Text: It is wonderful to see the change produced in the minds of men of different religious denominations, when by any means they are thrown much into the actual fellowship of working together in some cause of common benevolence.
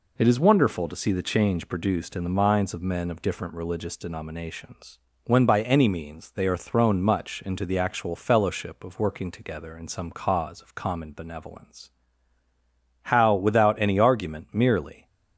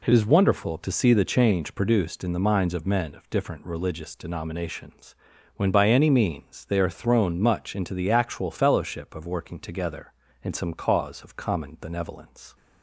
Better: second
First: goes on to say "How without any argument merely"; strong; from 13.0 s on; 2.0 s long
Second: none

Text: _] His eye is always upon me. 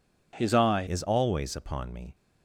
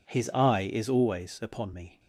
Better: second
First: changes voice at "is"; from 0.8 s on; 1.3 s long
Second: none

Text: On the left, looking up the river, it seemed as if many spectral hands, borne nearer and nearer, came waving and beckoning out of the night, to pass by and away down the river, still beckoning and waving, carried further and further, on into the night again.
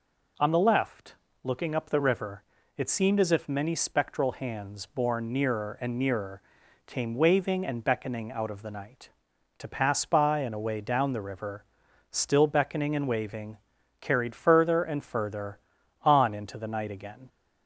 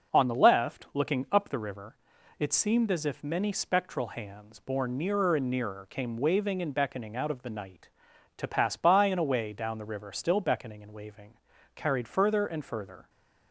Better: first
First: none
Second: stops before "on into the night again"; at 13.0 s

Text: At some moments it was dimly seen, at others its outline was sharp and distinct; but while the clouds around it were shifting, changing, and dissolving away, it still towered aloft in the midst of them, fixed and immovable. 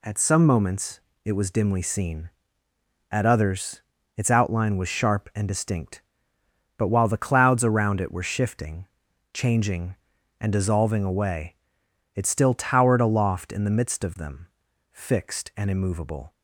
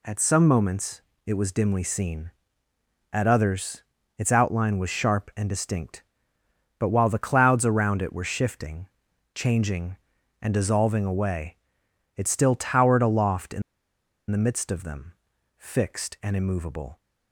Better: first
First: pauses between "moments" and "it"; slight; at 0.9 s; 0.26 s long // pauses between "others" and "its"; slight; at 3.8 s; 0.34 s long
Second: pauses between "moments" and "it"; slight; at 1.0 s; 0.26 s long // pauses between "others" and "its"; slight; at 3.8 s; 0.34 s long // pauses between "in" and "the"; noticeable; at 13.6 s; 0.68 s long

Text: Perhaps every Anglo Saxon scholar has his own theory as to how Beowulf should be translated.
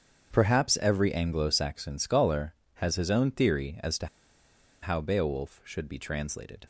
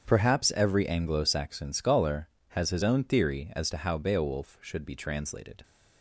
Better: second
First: starts louder than the rest; strong; until 1.3 s; 7.5 dB // pauses between "to" and "how"; noticeable; at 4.0 s; 0.76 s long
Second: starts louder than the rest; strong; until 1.0 s; 7.5 dB

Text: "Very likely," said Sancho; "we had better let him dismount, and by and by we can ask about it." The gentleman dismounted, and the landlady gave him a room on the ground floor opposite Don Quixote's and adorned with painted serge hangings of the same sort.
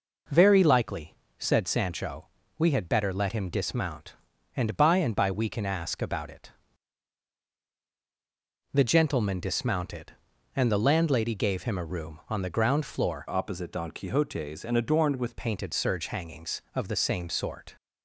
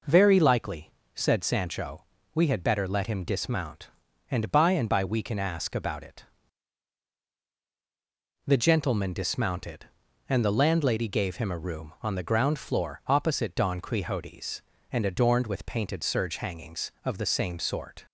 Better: second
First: changes voice from "opposite" to "with"; from 13.2 to 15.3 s; 2.1 s long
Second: none

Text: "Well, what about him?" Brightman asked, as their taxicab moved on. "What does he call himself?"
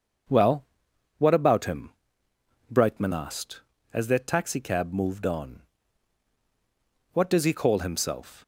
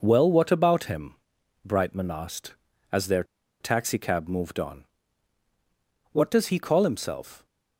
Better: first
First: none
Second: pauses between "their" and "taxicab"; at 3.2 s; 0.37 s long

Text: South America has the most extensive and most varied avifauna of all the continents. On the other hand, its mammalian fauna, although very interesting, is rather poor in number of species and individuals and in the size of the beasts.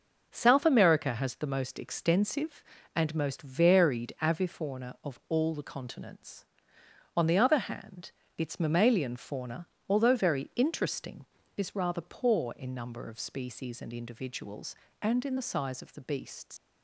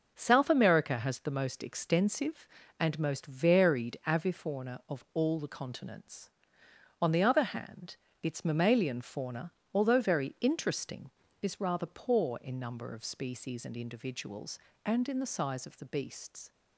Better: second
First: leaves "beasts" unfinished; at 16.5 s; 110 ms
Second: none

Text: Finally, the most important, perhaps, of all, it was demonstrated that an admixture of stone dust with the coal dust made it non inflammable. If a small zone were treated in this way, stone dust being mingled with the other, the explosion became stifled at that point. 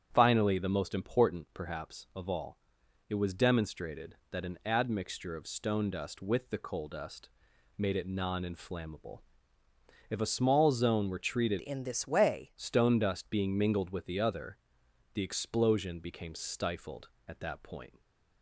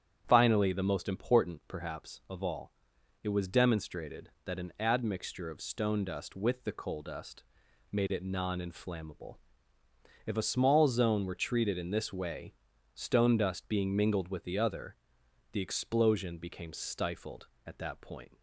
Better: second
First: starts louder than the rest; strong; until 1.1 s; 9 dB // pauses between "dust" and "made"; noticeable; at 7.2 s; 0.48 s long // changes voice from "in" to "way"; from 11.5 to 12.5 s; 1.0 s long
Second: starts louder than the rest; strong; until 1.2 s; 9 dB // pauses between "dust" and "made"; noticeable; at 7.4 s; 0.48 s long

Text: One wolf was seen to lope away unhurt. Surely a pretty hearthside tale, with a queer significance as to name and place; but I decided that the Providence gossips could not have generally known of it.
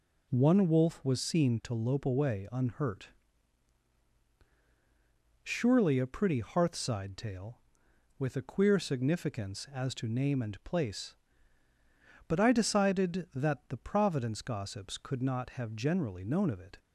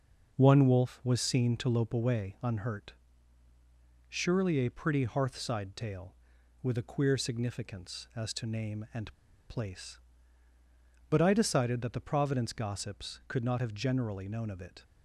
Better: first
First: none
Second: pauses between "and" and "place"; slight; at 9.1 s; 0.34 s long

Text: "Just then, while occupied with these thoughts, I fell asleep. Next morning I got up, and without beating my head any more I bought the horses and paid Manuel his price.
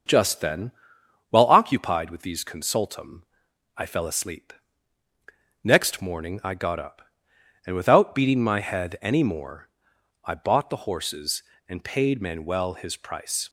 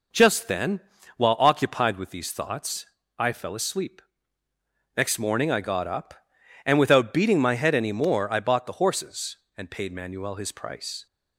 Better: second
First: starts louder than the rest; until 1.6 s; 6.5 dB // says "consultum" for "thoughts"; at 2.4 s // pauses between "more" and "I"; noticeable; at 9.6 s; 0.54 s long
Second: none

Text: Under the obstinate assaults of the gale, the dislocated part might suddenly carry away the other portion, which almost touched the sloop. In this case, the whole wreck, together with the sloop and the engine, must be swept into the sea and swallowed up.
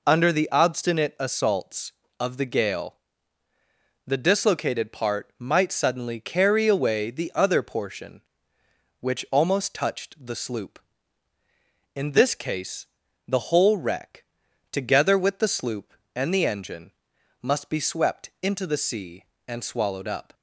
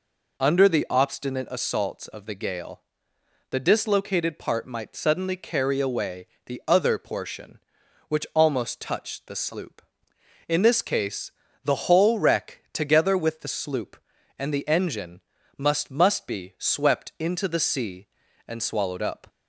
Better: first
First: none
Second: pauses between "away" and "the"; slight; at 6.2 s; 0.18 s long // says "must" twice; at 15.8 s

